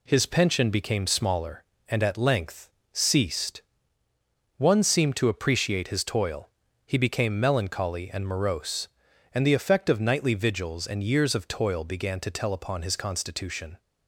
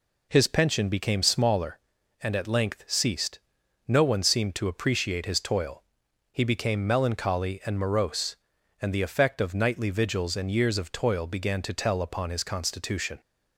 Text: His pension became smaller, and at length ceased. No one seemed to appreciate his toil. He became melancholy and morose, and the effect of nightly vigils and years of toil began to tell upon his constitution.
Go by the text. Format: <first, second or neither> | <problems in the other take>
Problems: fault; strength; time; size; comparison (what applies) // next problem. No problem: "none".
second | pauses between "length" and "ceased"; slight; at 2.6 s; 0.24 s long // skips "No"; at 4.0 s